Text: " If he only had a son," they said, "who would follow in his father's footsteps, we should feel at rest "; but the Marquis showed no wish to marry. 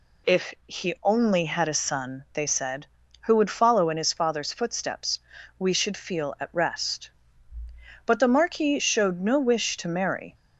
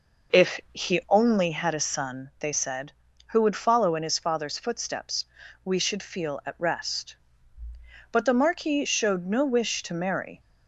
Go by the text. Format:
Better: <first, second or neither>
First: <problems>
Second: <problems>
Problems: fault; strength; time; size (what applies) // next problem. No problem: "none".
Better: first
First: none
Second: starts louder than the rest; noticeable; until 1.5 s; 5.5 dB